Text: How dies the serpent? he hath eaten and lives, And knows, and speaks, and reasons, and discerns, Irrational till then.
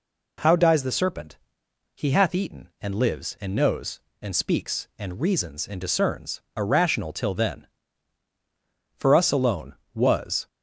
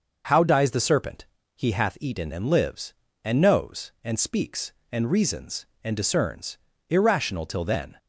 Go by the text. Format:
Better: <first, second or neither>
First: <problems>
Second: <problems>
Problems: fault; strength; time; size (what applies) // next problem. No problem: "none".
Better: second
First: goes on to say "For us alone Was"; from 8.9 s on; 1.5 s long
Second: none